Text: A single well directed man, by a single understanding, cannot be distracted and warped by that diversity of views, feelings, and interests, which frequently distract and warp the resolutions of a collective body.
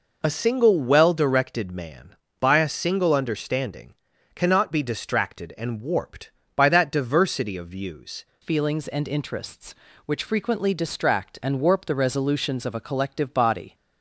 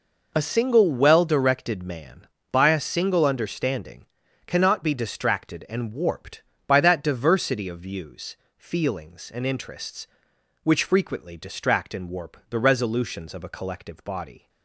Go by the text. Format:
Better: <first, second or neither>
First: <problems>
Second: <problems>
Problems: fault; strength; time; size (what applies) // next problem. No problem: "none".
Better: second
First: changes voice at "feelings"; from 8.4 s on; 5.3 s long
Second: none